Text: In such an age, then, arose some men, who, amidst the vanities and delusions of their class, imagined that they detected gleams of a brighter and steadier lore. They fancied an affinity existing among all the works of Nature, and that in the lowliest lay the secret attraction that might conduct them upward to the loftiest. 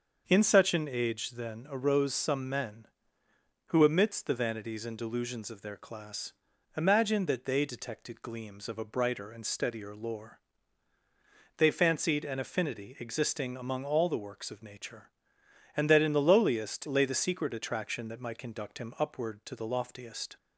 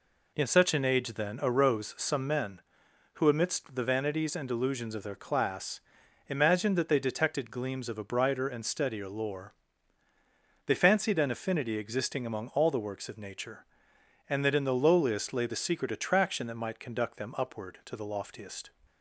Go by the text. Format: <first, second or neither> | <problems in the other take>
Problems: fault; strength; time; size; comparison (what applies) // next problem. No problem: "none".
second | starts louder than the rest; until 1.2 s; 6.5 dB // says "him" for "them"; at 18.7 s